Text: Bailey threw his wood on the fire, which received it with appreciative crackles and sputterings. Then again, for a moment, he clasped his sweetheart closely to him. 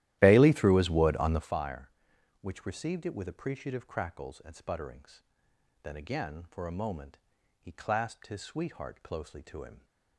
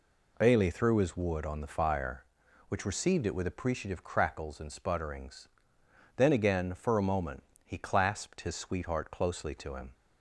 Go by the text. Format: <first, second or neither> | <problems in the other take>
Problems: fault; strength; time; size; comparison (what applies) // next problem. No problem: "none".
second | starts louder than the rest; strong; until 1.5 s; 14 dB